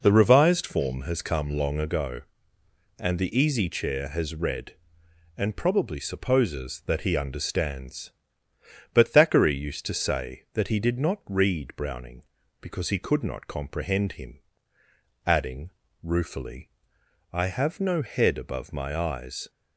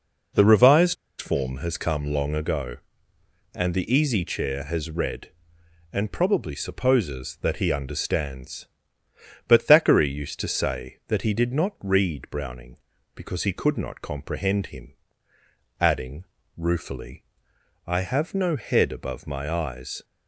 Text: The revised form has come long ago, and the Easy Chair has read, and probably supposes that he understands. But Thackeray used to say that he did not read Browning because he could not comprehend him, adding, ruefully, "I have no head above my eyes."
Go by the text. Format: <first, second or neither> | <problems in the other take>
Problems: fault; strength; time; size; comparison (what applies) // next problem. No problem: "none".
first | pauses between "revised" and "form"; slight; at 0.9 s; 0.24 s long